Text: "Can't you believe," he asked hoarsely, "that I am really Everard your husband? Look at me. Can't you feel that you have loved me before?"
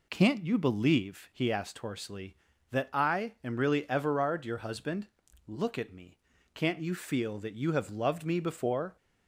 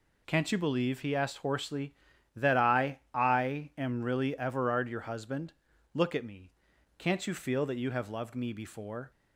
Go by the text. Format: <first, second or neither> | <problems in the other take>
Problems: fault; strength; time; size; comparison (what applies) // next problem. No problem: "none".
first | says "I" twice; at 3.1 s